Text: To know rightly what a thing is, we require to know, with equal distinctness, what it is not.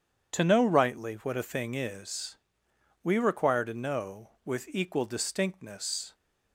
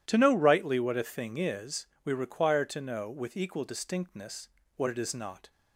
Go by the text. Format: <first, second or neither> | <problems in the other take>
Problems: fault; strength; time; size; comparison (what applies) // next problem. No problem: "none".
second | stops before "what it is not"; at 6.1 s